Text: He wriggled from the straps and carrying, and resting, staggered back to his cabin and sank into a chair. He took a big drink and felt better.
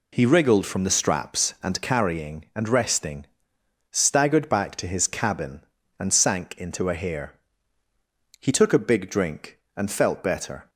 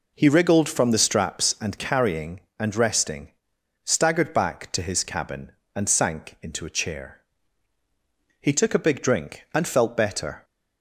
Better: second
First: says "hair" for "chair"; at 6.9 s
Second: none

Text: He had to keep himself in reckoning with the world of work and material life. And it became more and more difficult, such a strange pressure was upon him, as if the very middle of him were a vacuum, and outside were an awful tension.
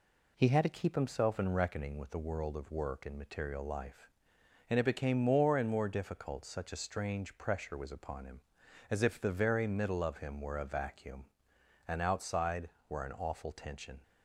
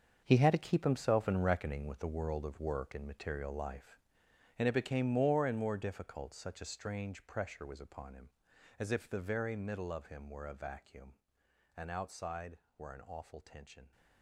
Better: first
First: none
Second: gets quieter; strong; throughout; 12 dB

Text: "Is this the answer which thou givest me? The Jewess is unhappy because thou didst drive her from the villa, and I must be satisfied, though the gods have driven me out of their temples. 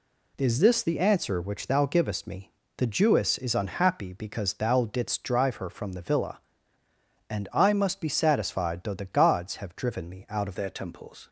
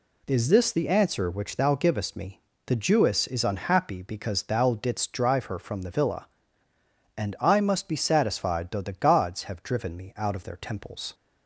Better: second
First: changes voice at "their"; from 10.5 s on; 0.7 s long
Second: none

